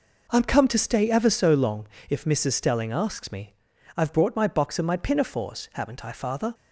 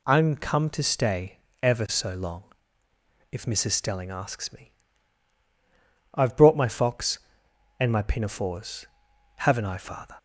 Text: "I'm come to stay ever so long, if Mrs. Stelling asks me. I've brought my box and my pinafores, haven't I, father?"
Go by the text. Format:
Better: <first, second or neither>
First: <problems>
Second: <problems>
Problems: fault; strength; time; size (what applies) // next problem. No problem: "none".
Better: first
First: none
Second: pauses between "stay" and "ever"; slight; at 1.3 s; 0.24 s long // says "fox" for "box"; at 6.6 s